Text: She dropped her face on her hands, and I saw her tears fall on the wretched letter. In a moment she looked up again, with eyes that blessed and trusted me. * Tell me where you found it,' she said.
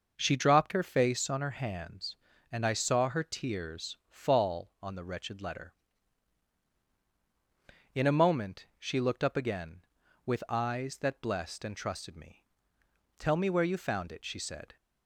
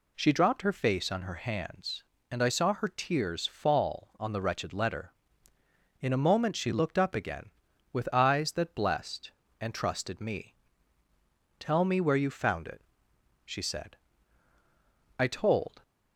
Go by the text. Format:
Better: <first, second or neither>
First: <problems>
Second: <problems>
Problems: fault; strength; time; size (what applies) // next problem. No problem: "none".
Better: first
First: none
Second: goes on to say "I told"; noticeable; from 15.1 s on; 0.64 s long